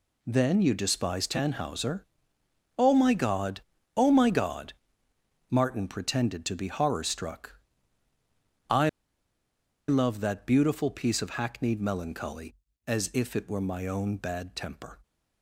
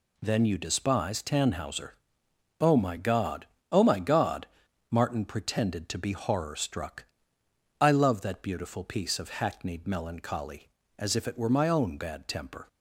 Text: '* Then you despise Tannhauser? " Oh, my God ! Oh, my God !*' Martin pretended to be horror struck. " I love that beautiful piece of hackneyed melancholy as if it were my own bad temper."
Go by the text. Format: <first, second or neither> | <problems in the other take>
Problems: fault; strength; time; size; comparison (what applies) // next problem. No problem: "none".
second | pauses between "I" and "love"; at 8.8 s; 0.99 s long